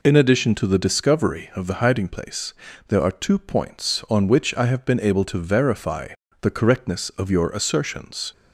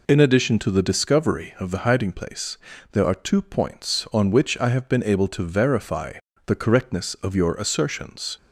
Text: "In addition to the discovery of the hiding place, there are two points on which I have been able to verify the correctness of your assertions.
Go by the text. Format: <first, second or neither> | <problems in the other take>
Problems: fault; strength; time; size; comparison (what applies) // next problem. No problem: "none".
neither | pauses between "verify" and "the"; slight; the same in both